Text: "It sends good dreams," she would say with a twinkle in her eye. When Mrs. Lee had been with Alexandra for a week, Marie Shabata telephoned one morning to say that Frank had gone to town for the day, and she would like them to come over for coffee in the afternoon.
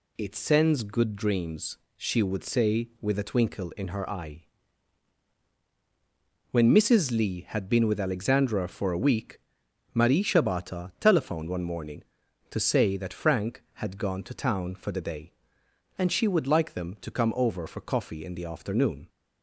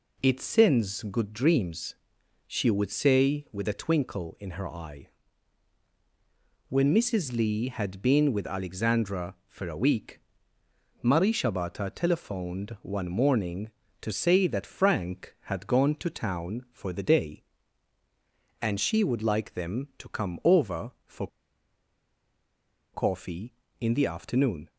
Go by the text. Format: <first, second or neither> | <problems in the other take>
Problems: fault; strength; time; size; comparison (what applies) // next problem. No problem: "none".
first | pauses between "for" and "coffee"; strong; at 21.2 s; 1.6 s long